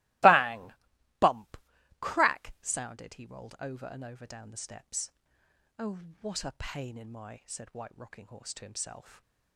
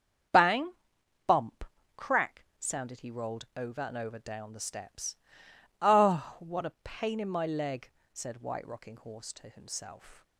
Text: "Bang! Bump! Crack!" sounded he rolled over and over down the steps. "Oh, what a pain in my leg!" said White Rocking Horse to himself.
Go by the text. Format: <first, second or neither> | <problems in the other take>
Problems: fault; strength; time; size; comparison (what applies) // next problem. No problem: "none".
second | starts louder than the rest; strong; until 2.1 s; 19 dB; strong in the second // skips "leg"; at 7.4 s // stays silent after the last word; slight; from 9.0 s on; 0.5 s long